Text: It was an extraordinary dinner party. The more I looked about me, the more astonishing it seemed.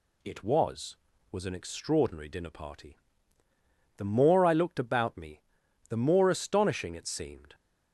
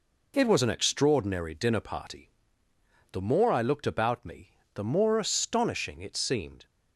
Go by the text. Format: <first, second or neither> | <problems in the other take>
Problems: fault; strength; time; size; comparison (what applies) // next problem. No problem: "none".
second | says "was" twice; at 1.3 s